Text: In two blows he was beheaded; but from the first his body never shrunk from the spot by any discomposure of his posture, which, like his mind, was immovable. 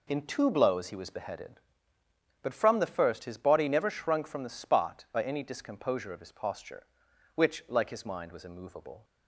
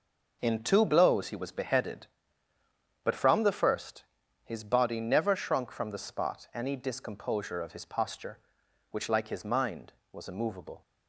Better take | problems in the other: first | pauses between "first" and "his"; at 4.0 s; 0.40 s long // skips "by"; at 6.5 s

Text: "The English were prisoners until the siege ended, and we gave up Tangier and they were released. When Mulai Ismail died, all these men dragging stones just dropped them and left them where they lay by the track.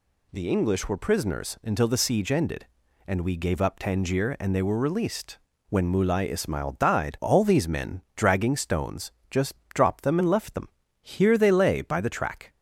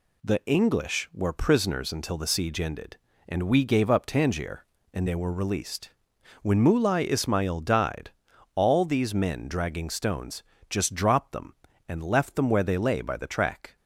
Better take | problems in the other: second | pauses between "stones" and "just"; slight; at 9.1 s; 0.20 s long; slight in the second // pauses between "just" and "dropped"; slight; at 9.5 s; 0.18 s long // says "here" for "where"; at 11.0 s

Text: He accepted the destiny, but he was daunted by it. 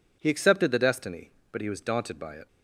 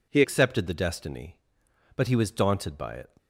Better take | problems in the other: first | changes voice at "accepted"; from 0.2 s on; 2.9 s long

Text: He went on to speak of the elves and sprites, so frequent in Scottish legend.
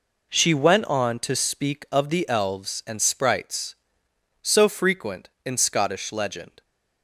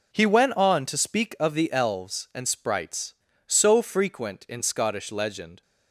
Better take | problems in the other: second | says "She" for "He"; at 0.2 s

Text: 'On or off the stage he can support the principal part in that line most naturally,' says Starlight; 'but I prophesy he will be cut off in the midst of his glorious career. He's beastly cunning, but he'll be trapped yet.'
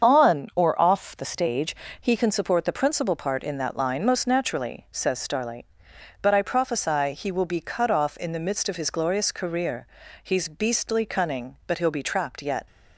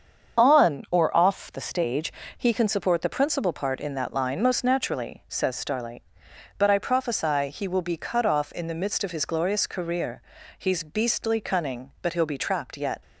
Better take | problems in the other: neither | starts louder than the rest; the same in both // pauses between "stage" and "he"; slight; the same in both

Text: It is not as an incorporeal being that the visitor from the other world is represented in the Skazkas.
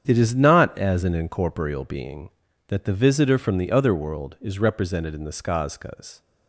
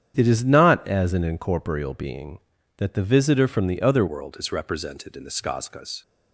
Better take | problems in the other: first | starts louder than the rest; strong; until 1.1 s; 9 dB; strong in the first // changes voice at "world"; from 4.0 s on; 2.0 s long

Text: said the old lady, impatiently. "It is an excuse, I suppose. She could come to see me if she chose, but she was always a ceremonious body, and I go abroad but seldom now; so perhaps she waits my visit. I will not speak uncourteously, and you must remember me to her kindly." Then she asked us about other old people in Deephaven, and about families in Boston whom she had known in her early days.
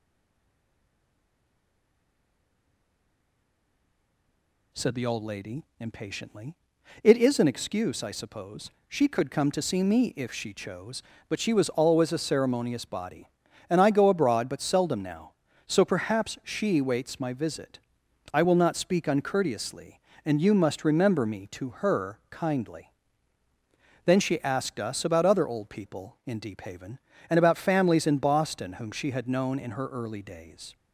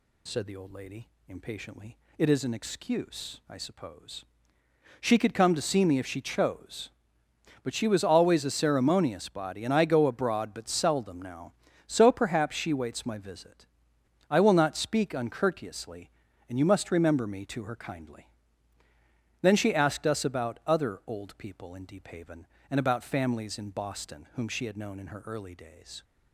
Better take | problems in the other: second | stays silent before the first word; strong; until 4.7 s; 4.7 s long

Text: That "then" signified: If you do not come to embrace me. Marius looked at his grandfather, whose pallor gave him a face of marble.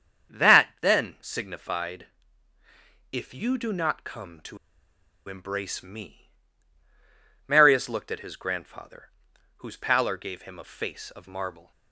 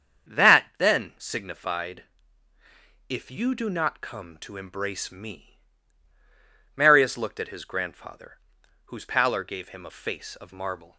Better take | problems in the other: second | starts louder than the rest; strong; until 1.4 s; 7.5 dB; strong in the second // pauses between "to" and "embrace"; noticeable; at 4.5 s; 0.71 s long

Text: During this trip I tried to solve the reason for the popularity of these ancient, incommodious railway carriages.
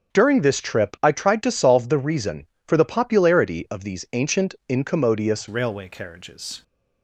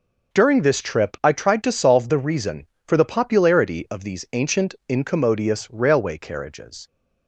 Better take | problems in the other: second | starts louder than the rest; strong; until 1.2 s; 7 dB // changes voice at "railway"; from 5.4 s on; 1.2 s long

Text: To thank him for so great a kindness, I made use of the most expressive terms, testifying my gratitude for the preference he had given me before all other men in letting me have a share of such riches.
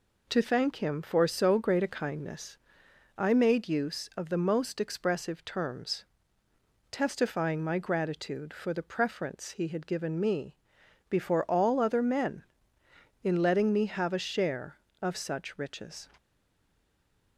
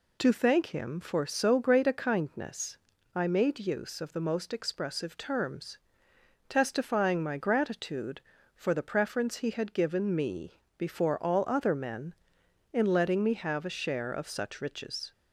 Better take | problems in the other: second | pauses between "me" and "before"; noticeable; at 10.5 s; 0.54 s long; slight in the second // stays silent after the last word; noticeable; from 16.1 s on; 1.2 s long

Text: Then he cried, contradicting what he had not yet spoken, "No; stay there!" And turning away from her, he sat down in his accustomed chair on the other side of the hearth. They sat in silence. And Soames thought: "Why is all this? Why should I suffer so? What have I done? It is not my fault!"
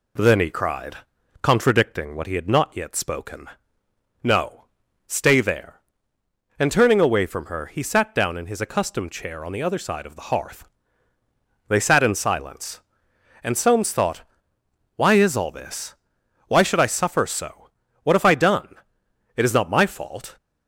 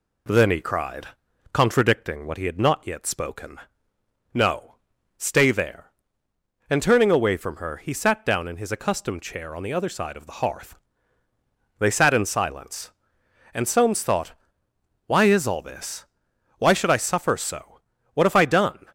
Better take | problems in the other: first | stops before "It is not my fault"; at 18.8 s

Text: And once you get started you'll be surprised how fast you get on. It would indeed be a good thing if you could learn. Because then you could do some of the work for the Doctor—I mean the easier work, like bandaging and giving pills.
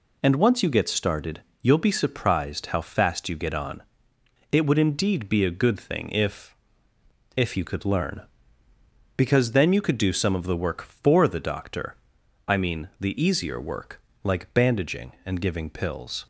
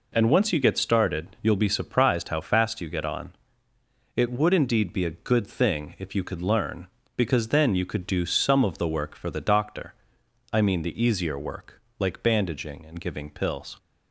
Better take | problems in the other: second | pauses between "started" and "you'll"; slight; at 1.4 s; 0.18 s long // says "if" twice; at 7.3 s

